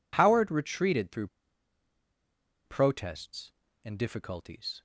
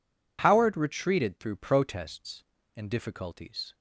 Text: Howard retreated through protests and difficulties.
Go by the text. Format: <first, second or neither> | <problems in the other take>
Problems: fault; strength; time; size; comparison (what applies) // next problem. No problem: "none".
second | pauses between "through" and "protests"; strong; at 1.2 s; 1.3 s long